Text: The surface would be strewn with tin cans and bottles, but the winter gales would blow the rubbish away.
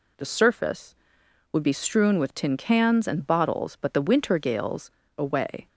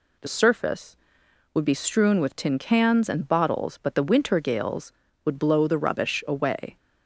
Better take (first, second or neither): second